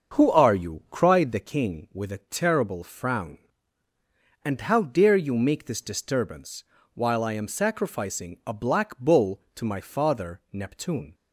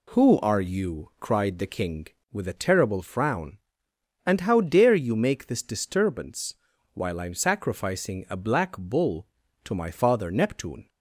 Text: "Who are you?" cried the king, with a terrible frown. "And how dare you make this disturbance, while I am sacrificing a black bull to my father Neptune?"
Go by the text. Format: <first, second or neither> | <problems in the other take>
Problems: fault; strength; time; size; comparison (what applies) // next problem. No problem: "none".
second | starts louder than the rest; until 1.6 s; 7 dB